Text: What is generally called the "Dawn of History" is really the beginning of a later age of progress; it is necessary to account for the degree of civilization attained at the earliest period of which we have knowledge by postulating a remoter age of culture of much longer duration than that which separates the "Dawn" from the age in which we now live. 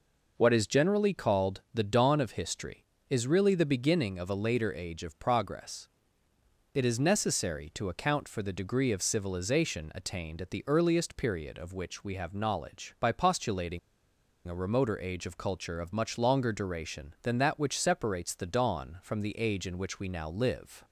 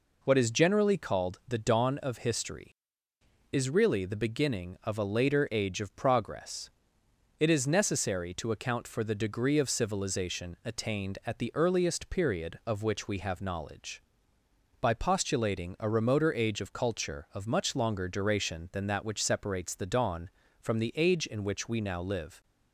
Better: second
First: pauses between "postulating" and "a"; noticeable; at 13.7 s; 0.68 s long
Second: none

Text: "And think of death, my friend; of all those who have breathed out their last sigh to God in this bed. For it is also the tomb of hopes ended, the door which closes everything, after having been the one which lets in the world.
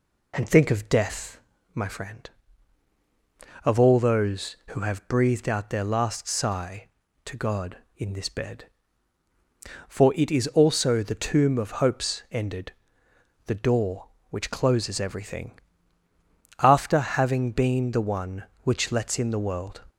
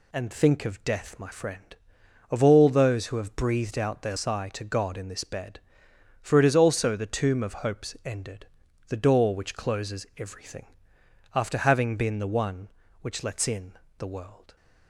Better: first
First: none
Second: skips "last"; at 4.1 s // pauses between "in" and "the"; slight; at 13.7 s; 0.26 s long

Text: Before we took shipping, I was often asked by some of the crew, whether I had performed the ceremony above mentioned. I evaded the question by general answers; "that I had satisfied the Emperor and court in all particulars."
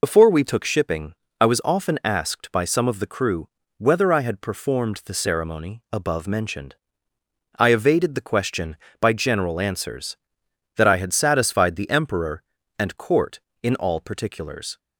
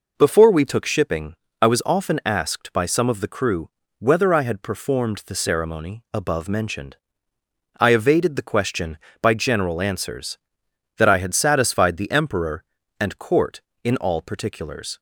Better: second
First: loses the start of "Before"; at 0.0 s; 70 ms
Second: none

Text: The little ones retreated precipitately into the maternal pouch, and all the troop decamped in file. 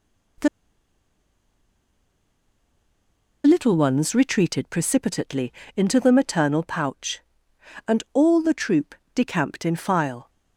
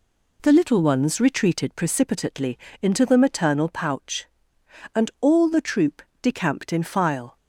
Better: second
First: pauses between "The" and "little"; strong; at 0.4 s; 2.9 s long // pauses between "precipitately" and "into"; slight; at 5.5 s; 0.24 s long // pauses between "troop" and "decamped"; slight; at 8.9 s; 0.18 s long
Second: pauses between "precipitately" and "into"; slight; at 2.5 s; 0.24 s long // pauses between "troop" and "decamped"; slight; at 6.0 s; 0.18 s long

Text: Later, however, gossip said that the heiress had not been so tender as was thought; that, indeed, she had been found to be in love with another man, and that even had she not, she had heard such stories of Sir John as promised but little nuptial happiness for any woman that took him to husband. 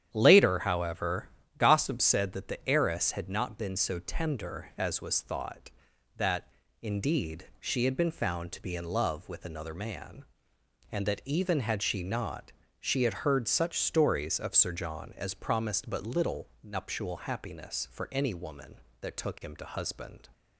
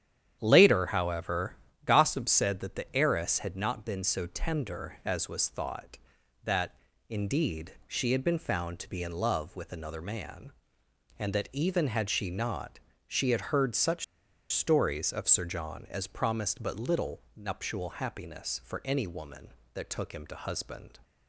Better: first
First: starts louder than the rest; strong; until 1.1 s; 9.5 dB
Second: starts louder than the rest; strong; until 1.4 s; 9.5 dB // pauses between "such" and "stories"; noticeable; at 14.0 s; 0.47 s long

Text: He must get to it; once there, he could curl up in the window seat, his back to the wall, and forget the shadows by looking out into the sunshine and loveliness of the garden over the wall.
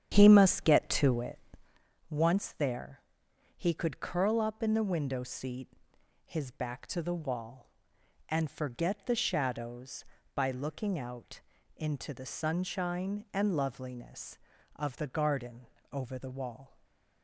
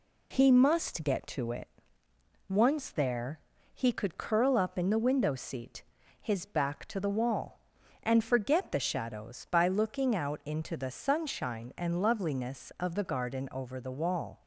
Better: second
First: starts louder than the rest; strong; until 1.8 s; 9.5 dB // pauses between "out" and "into"; slight; at 11.4 s; 0.36 s long // pauses between "garden" and "over"; slight; at 15.6 s; 0.26 s long // stays silent after the last word; slight; from 16.6 s on; 0.6 s long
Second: none

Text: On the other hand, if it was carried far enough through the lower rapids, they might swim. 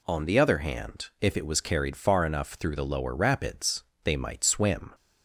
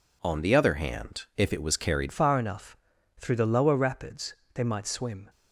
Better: first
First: none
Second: changes voice at "far"; from 2.1 s on; 3.1 s long // pauses between "enough" and "through"; at 2.7 s; 0.42 s long

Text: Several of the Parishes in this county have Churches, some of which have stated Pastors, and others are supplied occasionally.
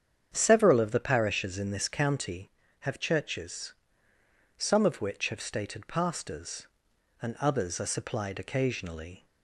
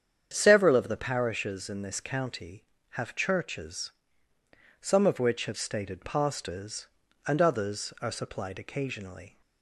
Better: neither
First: starts louder than the rest; strong; until 1.3 s; 8 dB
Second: starts louder than the rest; strong; until 1.3 s; 8.5 dB

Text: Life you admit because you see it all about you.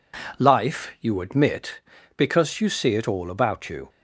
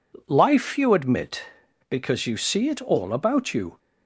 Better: neither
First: none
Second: none

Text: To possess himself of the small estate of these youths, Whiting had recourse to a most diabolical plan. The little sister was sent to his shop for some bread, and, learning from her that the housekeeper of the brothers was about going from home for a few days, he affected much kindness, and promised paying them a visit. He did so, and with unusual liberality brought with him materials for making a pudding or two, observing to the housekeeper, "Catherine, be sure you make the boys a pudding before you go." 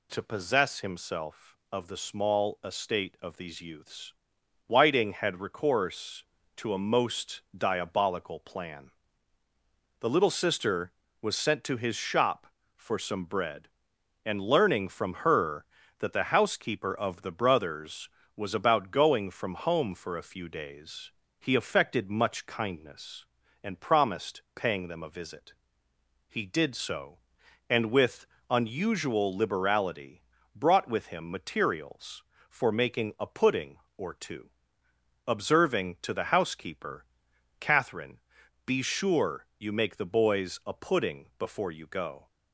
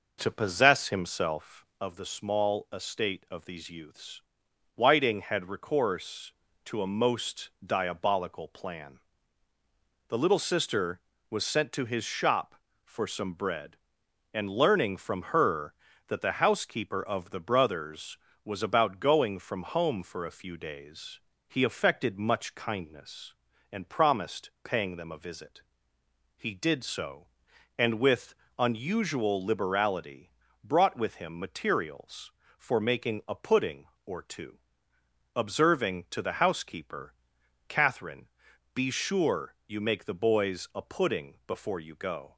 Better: first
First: pauses between "with" and "unusual"; slight; at 28.2 s; 0.26 s long // pauses between "liberality" and "brought"; slight; at 30.2 s; 0.34 s long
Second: starts louder than the rest; noticeable; until 1.8 s; 5.5 dB // pauses between "with" and "unusual"; slight; at 28.3 s; 0.26 s long // pauses between "liberality" and "brought"; slight; at 30.3 s; 0.34 s long

